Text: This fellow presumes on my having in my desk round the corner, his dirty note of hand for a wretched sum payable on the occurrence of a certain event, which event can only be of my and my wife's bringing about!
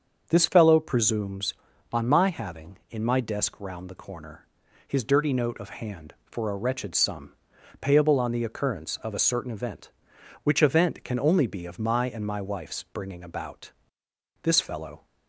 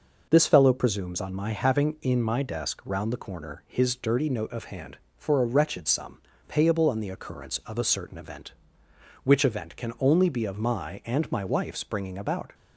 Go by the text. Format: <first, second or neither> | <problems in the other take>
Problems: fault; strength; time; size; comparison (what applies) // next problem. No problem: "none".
second | starts louder than the rest; until 1.3 s; 7 dB // pauses between "sum" and "payable"; noticeable; at 7.3 s; 0.46 s long; slight in the second // goes on to say "This fellow"; noticeable; from 14.4 s on; 0.62 s long